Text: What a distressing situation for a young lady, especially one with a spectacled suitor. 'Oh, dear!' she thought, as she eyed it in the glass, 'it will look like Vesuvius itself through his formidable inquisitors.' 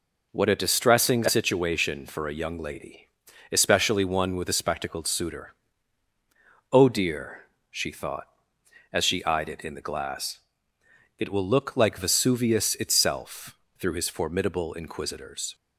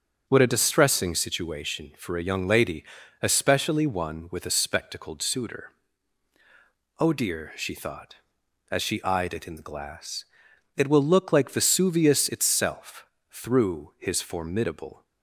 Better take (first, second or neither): first